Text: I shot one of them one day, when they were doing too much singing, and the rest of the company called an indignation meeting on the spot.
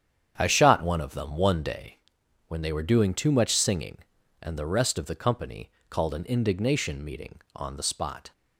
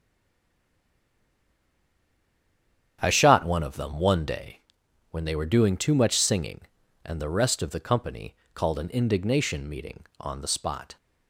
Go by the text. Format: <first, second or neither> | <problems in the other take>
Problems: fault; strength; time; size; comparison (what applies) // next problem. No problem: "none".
first | stays silent before the first word; strong; until 2.9 s; 2.9 s long // starts louder than the rest; strong; until 4.0 s; 9 dB; strong in the first // pauses between "company" and "called"; slight; at 8.3 s; 0.20 s long; slight in the first